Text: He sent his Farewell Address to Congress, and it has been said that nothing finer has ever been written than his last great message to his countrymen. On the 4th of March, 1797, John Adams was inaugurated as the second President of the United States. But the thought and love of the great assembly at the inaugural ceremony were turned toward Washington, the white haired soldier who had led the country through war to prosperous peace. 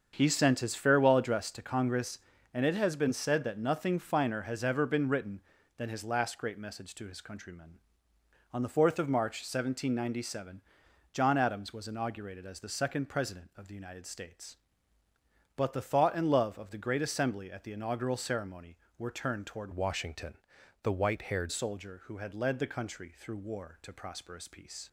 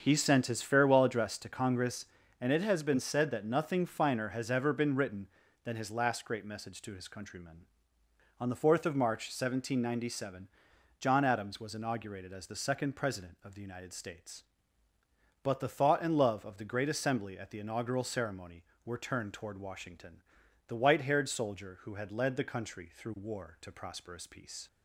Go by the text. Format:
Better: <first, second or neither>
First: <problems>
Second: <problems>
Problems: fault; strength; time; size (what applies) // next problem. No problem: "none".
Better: second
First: starts louder than the rest; until 1.1 s; 7 dB // changes voice from "Washington" to "haired"; from 19.7 to 21.5 s; 1.8 s long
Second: starts louder than the rest; until 1.0 s; 7 dB